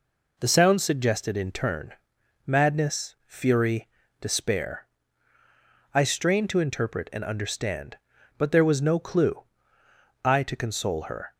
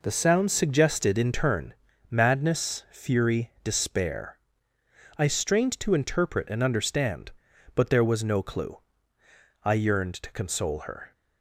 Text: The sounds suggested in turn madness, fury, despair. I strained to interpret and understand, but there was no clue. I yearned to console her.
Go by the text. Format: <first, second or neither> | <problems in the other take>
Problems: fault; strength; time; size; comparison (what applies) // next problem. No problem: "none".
second | pauses between "turn" and "madness"; noticeable; at 1.9 s; 0.52 s long; slight in the second // skips "yearned"; at 10.4 s